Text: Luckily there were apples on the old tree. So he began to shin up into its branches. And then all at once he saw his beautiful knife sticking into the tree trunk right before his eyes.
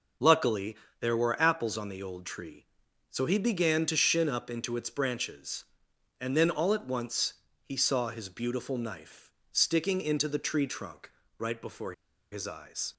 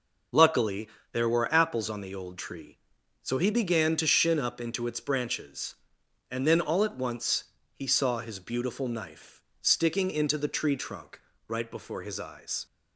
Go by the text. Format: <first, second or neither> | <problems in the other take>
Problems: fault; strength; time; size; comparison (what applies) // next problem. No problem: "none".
second | pauses between "Luckily" and "there"; slight; at 0.7 s; 0.24 s long; slight in the second // pauses between "once" and "he"; slight; at 7.3 s; 0.30 s long; slight in the second // pauses between "knife" and "sticking"; slight; at 9.2 s; 0.22 s long; slight in the second // pauses between "trunk" and "right"; slight; at 11.0 s; 0.28 s long; slight in the second // pauses between "before" and "his"; at 11.9 s; 0.39 s long